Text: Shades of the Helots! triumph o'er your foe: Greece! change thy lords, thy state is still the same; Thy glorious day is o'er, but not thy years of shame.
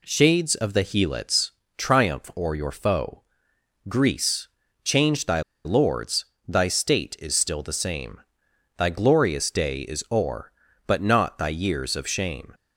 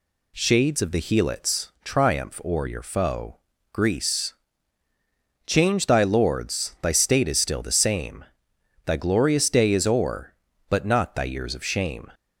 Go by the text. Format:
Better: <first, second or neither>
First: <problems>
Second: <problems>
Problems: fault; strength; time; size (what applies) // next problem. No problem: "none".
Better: second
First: pauses between "thy" and "lords"; slight; at 5.4 s; 0.24 s long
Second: none